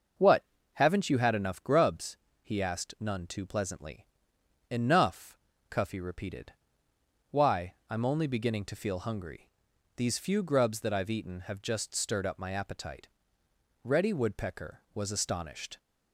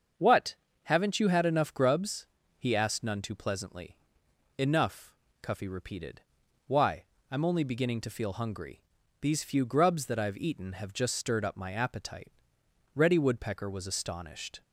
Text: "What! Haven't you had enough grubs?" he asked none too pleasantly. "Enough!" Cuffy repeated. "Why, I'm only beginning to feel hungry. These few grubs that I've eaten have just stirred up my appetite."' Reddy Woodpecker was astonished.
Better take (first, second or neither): neither